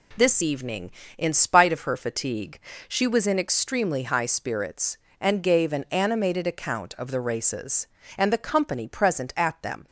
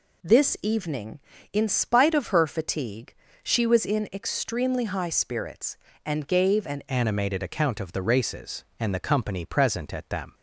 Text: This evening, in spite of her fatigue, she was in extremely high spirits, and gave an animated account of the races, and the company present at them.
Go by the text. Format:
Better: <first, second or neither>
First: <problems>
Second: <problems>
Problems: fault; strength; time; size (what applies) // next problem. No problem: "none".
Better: first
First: none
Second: changes voice at "animated"; from 6.8 s on; 3.5 s long